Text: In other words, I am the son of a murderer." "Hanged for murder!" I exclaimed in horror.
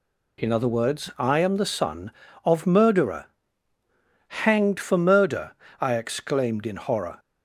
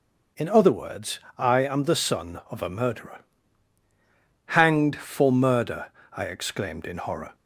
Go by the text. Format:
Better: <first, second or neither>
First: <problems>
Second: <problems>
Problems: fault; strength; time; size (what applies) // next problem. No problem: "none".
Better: second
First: skips "a"; at 2.6 s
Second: none